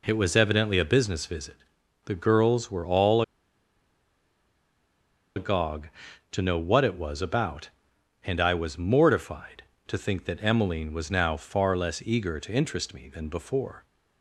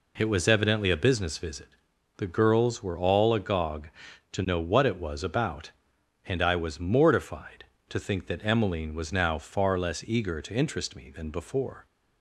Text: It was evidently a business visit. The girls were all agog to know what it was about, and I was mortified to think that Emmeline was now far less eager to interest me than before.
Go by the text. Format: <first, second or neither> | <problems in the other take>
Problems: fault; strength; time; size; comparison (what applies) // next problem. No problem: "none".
second | pauses between "all" and "agog"; strong; at 3.2 s; 2.1 s long